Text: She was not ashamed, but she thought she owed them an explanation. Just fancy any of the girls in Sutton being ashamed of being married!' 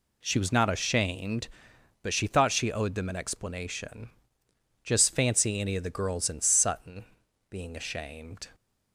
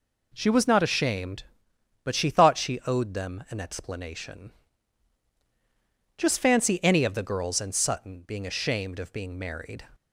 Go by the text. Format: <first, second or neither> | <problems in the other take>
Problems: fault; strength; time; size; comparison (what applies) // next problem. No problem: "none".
second | pauses between "Sutton" and "being"; at 7.0 s; 0.44 s long // stops before "of being married"; at 8.5 s